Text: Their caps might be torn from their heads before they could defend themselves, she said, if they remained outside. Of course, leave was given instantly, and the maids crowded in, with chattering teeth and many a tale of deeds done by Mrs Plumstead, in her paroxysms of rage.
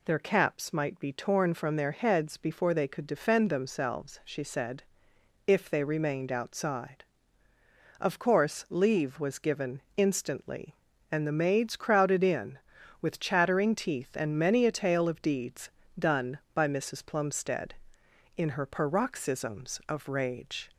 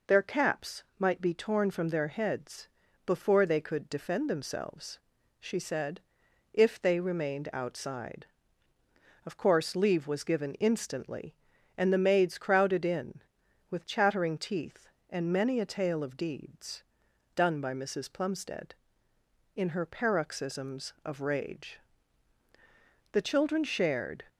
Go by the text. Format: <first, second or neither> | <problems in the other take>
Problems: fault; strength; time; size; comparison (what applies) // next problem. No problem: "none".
first | pauses between "heads" and "before"; at 2.6 s; 0.38 s long // pauses between "deeds" and "done"; noticeable; at 16.8 s; 0.52 s long; slight in the first // goes on to say "The children shared"; noticeable; from 23.1 s on; 1.1 s long